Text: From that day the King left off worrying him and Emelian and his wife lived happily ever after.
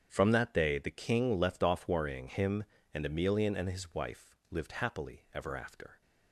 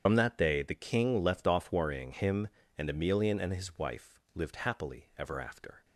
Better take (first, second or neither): first